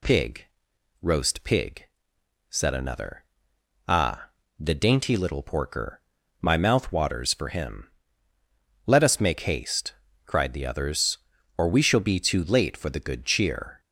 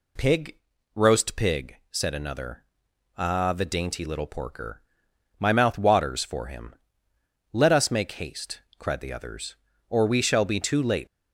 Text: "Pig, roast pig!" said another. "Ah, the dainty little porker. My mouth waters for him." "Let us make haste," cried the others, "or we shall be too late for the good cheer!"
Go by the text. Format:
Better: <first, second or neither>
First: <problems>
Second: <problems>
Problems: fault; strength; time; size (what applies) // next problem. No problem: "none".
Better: first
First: none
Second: stops before "for the good cheer"; at 11.0 s